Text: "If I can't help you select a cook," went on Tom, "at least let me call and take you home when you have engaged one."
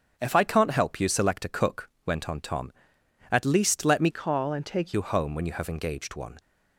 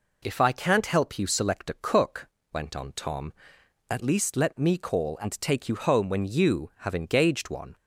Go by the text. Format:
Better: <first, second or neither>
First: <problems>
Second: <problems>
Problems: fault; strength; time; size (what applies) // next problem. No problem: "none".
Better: second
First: starts louder than the rest; until 1.1 s; 7 dB // changes voice from "call" to "take"; from 4.1 to 4.9 s; 0.8 s long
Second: none